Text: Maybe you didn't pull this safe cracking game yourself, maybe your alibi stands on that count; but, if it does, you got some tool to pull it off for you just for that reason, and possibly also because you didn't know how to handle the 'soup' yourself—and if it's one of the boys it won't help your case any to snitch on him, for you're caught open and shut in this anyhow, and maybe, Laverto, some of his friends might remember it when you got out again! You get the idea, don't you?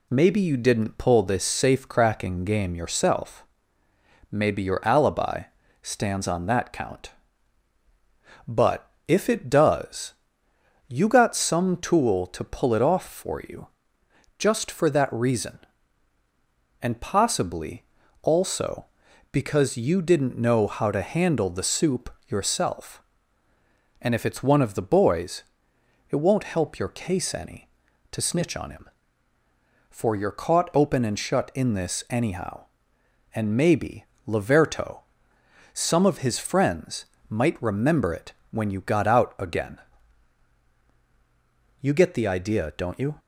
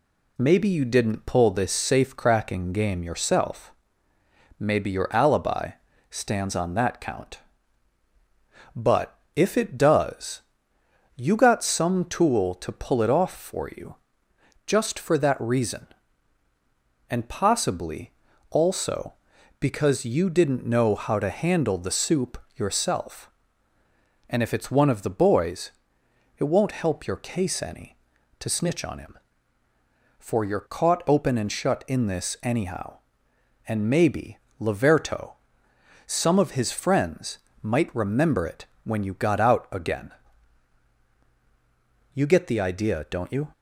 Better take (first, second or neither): neither